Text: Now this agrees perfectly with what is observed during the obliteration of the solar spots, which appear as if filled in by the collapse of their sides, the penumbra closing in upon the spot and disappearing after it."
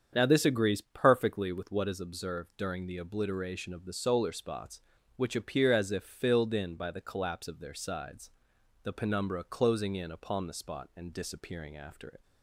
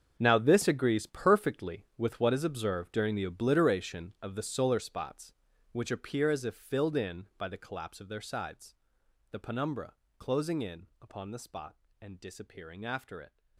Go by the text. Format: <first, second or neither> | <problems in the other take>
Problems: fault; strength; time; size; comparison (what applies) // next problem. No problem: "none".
first | gets quieter; strong; throughout; 13.5 dB // starts louder than the rest; strong; until 1.2 s; 7.5 dB; strong in the first // pauses between "penumbra" and "closing"; slight; at 9.9 s; 0.26 s long // pauses between "in" and "upon"; slight; at 10.8 s; 0.16 s long